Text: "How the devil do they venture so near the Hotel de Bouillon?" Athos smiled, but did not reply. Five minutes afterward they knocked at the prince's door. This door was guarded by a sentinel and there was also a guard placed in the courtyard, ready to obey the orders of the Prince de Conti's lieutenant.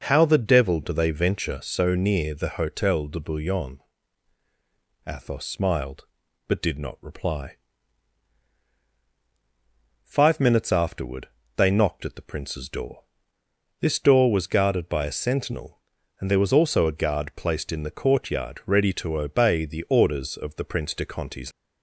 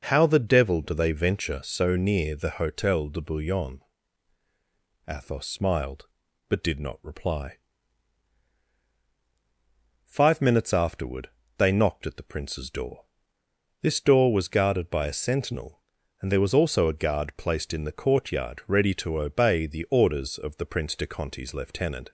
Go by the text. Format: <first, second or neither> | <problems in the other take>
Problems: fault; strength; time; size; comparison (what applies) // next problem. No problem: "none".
second | pauses between "afterward" and "they"; slight; at 11.2 s; 0.26 s long; slight in the second // stops before "lieutenant"; at 21.5 s